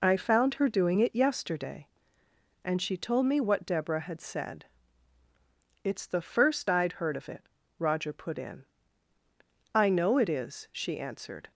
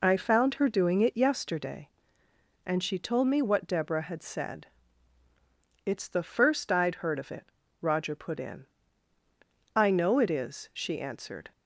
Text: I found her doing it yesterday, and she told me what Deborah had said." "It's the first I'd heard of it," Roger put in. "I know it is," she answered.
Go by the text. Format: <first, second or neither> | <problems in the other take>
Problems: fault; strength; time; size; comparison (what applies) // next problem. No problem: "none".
neither | none